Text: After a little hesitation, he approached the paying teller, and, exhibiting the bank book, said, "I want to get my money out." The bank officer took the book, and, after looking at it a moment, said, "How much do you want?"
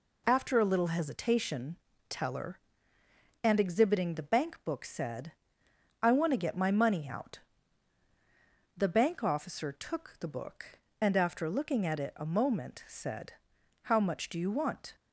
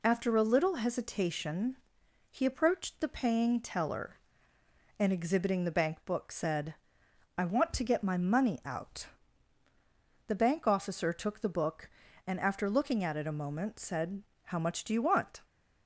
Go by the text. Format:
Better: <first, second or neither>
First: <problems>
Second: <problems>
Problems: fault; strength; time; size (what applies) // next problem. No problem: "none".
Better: second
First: skips "he approached the paying"; at 1.9 s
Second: none